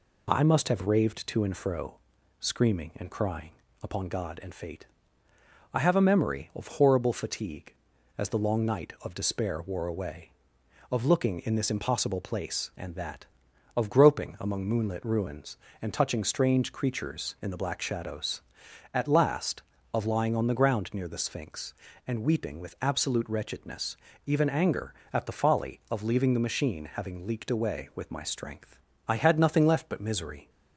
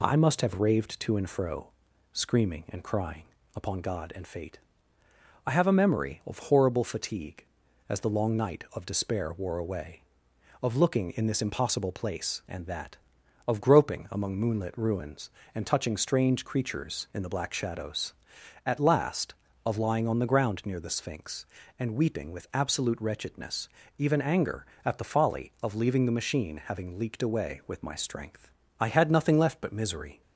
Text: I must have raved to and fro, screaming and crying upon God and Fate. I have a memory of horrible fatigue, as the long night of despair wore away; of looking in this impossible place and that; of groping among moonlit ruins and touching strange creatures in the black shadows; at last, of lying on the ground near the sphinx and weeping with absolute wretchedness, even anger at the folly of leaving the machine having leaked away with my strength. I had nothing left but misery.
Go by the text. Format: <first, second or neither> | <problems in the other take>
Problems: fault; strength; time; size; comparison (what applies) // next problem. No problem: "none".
neither | pauses between "crying" and "upon"; slight; the same in both